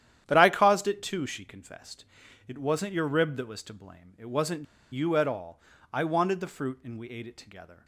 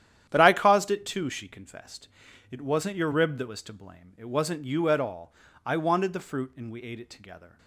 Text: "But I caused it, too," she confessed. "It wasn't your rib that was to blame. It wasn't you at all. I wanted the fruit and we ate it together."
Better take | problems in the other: second | starts louder than the rest; strong; until 1.2 s; 10.5 dB; strong in the second // pauses between "wasn't" and "you"; slight; at 4.6 s; 0.27 s long

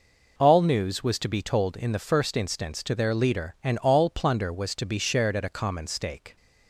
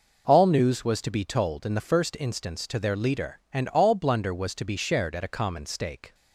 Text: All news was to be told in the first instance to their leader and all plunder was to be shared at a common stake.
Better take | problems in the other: first | says "blunder" for "plunder"; at 3.9 s

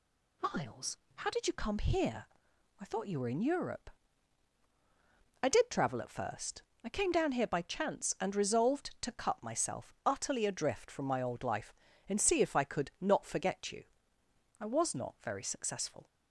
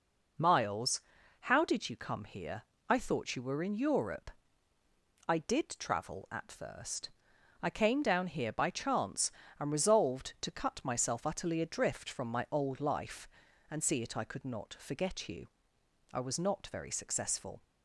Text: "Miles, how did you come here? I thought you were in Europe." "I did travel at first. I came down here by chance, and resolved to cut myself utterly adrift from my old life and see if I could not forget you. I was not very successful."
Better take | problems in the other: first | says "it" for "if"; at 14.0 s

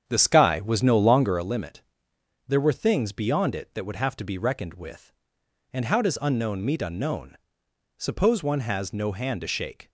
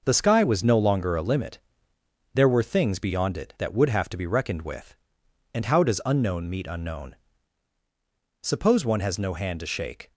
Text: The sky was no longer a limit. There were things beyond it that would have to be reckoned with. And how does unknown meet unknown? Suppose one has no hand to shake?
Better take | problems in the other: second | starts louder than the rest; strong; until 1.5 s; 8.5 dB

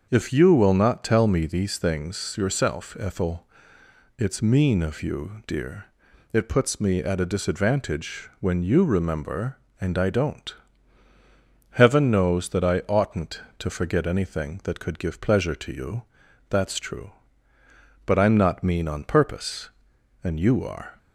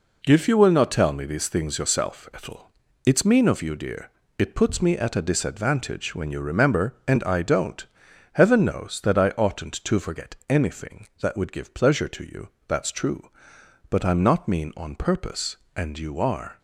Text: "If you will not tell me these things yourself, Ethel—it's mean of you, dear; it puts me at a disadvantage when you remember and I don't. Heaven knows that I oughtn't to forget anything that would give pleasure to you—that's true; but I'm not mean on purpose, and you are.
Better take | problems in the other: second | starts louder than the rest; until 1.1 s; 6.5 dB // says "could" for "would"; at 14.8 s

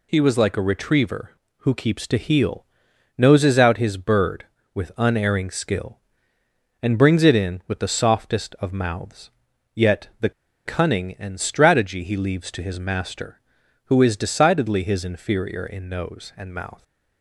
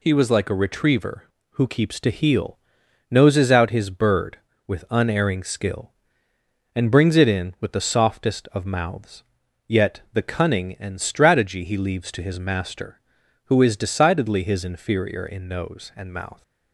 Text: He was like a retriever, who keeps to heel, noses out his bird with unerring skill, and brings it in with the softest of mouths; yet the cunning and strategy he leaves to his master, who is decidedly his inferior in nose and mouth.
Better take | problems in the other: second | pauses between "the" and "cunning"; slight; at 10.3 s; 0.34 s long

